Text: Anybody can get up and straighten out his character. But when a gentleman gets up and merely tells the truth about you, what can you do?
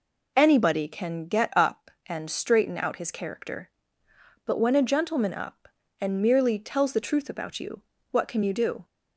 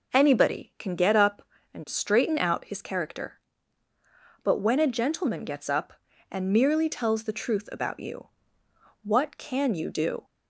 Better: second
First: skips "gets"; at 5.3 s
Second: none

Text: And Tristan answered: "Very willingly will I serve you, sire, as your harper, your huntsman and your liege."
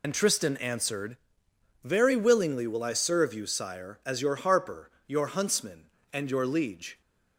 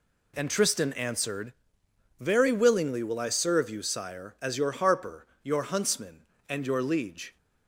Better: second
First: loses the start of "And"; at 0.0 s; 70 ms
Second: none

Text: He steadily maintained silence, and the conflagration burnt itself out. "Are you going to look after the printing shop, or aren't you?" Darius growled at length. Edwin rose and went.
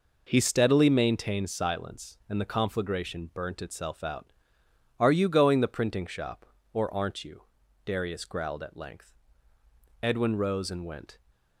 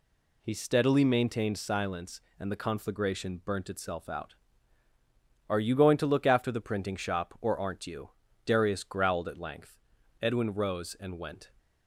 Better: second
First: skips "to look after"; at 5.6 s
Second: none

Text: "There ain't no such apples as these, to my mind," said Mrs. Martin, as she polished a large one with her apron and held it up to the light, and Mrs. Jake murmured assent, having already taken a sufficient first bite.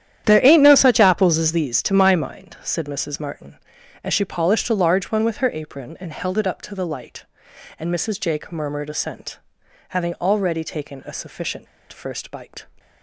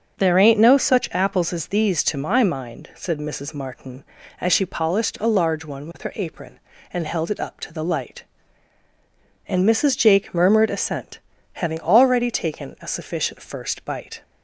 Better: second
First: starts louder than the rest; strong; until 1.2 s; 10.5 dB // pauses between "sufficient" and "first"; slight; at 11.6 s; 0.26 s long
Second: starts louder than the rest; until 1.1 s; 6.5 dB

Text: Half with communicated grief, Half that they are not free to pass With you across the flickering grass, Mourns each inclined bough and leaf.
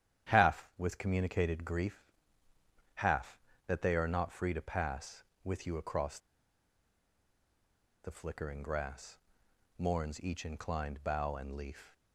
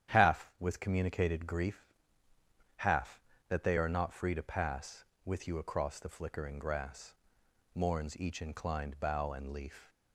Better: second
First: starts louder than the rest; strong; until 1.3 s; 10 dB // pauses between "across" and "the"; strong; at 6.1 s; 1.8 s long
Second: starts louder than the rest; strong; until 1.1 s; 10 dB

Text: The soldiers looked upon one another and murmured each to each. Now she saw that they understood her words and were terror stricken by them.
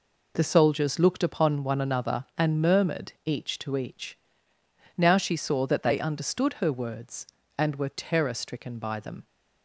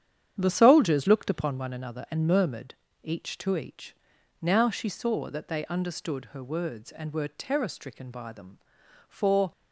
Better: first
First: none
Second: starts louder than the rest; strong; until 1.4 s; 9 dB // pauses between "murmured" and "each"; slight; at 2.7 s; 0.26 s long // goes on to say "For"; slight; from 9.0 s on; 0.44 s long

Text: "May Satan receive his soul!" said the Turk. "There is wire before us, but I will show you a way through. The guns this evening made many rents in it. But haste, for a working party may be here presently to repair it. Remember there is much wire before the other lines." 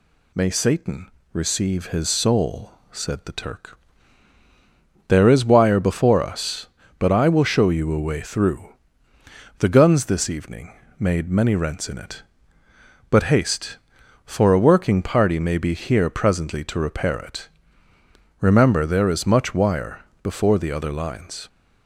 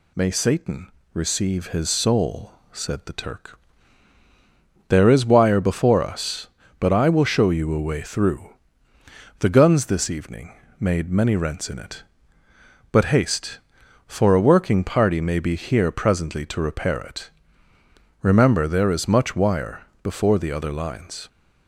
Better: neither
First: pauses between "Satan" and "receive"; slight; at 1.0 s; 0.24 s long // pauses between "evening" and "made"; slight; at 10.7 s; 0.28 s long // pauses between "wire" and "before"; slight; at 20.0 s; 0.20 s long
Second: pauses between "Satan" and "receive"; slight; at 0.8 s; 0.24 s long // pauses between "evening" and "made"; slight; at 10.5 s; 0.28 s long // pauses between "wire" and "before"; slight; at 19.8 s; 0.18 s long

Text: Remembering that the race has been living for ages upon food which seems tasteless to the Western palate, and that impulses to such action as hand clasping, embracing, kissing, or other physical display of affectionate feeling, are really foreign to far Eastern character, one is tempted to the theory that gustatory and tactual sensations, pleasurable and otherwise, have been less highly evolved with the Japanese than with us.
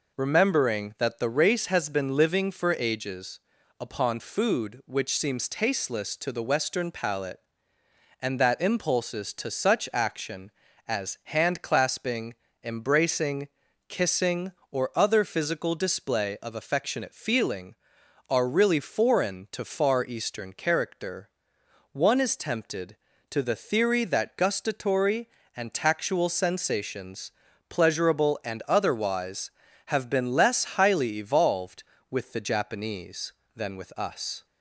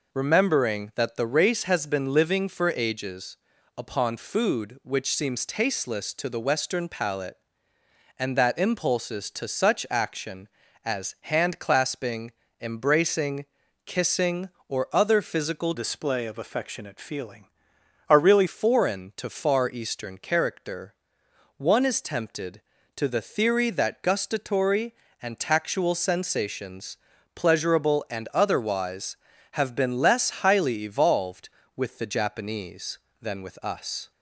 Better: first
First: pauses between "ages" and "upon"; at 3.3 s; 0.40 s long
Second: pauses between "ages" and "upon"; at 3.3 s; 0.40 s long // changes voice from "display" to "really"; from 15.7 to 18.4 s; 2.7 s long

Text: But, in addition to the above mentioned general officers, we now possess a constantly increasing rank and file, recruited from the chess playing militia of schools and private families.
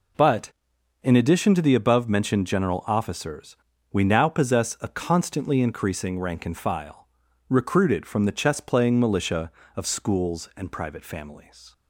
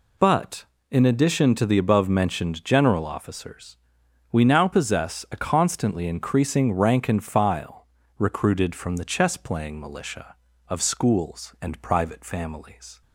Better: neither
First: none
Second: none

